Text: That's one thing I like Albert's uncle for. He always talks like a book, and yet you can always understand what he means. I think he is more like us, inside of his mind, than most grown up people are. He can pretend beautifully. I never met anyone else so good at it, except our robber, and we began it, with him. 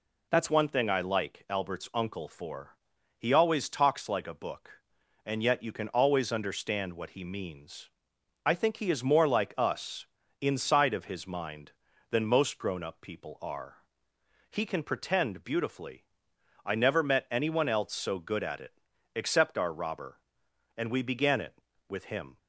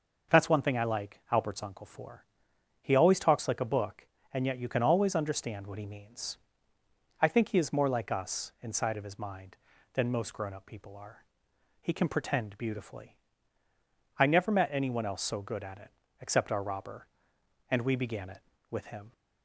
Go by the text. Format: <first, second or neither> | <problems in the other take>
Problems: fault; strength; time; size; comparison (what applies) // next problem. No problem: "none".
second | changes voice at "one"; from 0.4 s on; 21.9 s long